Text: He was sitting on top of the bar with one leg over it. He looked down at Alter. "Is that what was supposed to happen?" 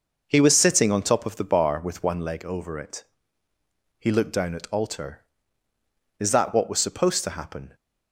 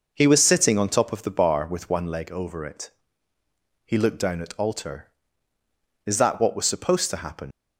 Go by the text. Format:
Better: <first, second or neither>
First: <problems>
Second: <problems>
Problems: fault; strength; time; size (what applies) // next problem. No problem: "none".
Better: first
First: none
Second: leaves "happen" unfinished; at 7.5 s; 105 ms